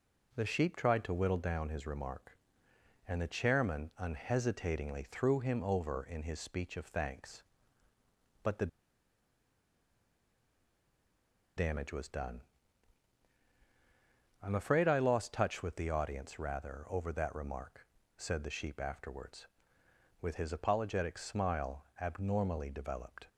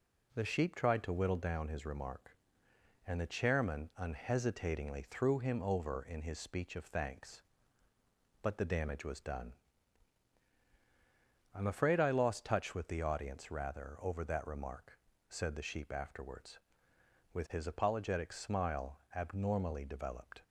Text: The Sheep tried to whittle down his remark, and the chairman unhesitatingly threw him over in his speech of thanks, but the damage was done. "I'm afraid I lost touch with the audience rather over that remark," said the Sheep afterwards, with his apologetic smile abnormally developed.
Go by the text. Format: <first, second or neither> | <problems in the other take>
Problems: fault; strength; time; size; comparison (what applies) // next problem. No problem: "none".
second | pauses between "the" and "damage"; strong; at 8.6 s; 2.8 s long // pauses between "smile" and "abnormally"; slight; at 21.8 s; 0.16 s long; slight in the second